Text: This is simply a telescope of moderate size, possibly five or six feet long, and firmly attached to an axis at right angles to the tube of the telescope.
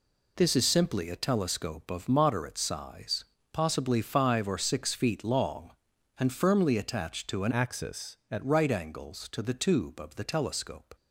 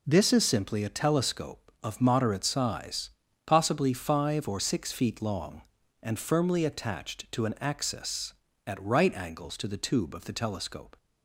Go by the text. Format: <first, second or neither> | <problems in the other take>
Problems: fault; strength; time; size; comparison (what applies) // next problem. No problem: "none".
second | changes voice from "axis" to "at"; from 7.5 to 8.4 s; 0.9 s long